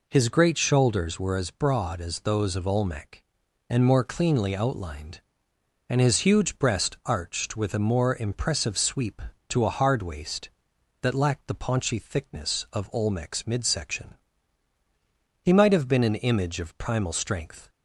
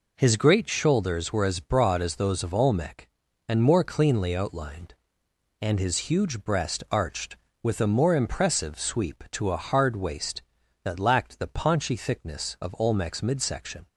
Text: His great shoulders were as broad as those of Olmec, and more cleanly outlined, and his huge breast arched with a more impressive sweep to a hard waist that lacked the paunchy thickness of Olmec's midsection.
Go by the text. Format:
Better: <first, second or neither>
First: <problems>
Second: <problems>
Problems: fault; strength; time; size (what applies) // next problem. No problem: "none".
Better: second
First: goes on to say "He might have been an image of primal strength"; strong; from 15.4 s on; 2.2 s long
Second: none